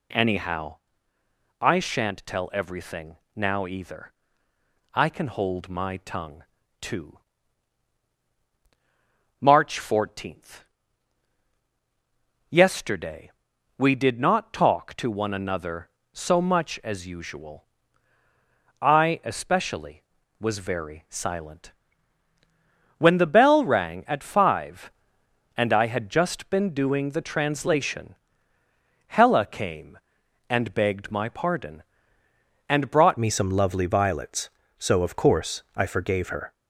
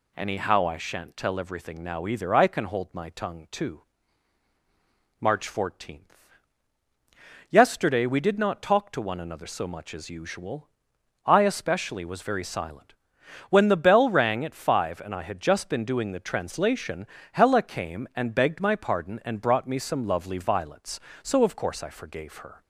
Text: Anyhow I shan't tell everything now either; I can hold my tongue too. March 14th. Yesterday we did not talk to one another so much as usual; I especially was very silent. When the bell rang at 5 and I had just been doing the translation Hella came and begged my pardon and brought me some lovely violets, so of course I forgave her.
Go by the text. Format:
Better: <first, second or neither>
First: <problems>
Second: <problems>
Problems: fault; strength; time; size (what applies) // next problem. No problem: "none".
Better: second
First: pauses between "Anyhow" and "I"; noticeable; at 0.7 s; 0.86 s long // pauses between "everything" and "now"; slight; at 3.1 s; 0.18 s long // pauses between "tongue" and "too"; at 6.4 s; 0.38 s long // pauses between "Yesterday" and "we"; noticeable; at 13.2 s; 0.48 s long // pauses between "translation" and "Hella"; noticeable; at 28.1 s; 0.92 s long // changes voice at "me"; from 33.1 s on; 3.4 s long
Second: pauses between "translation" and "Hella"; slight; at 17.0 s; 0.24 s long